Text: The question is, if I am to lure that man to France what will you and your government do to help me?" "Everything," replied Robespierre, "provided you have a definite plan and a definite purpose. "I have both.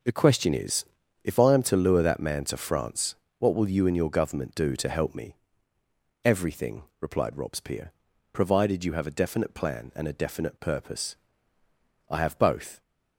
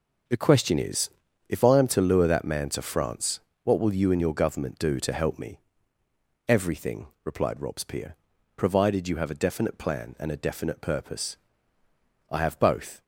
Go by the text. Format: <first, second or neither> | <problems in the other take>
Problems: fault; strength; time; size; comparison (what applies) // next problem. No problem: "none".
neither | pauses between "France" and "what"; slight; the same in both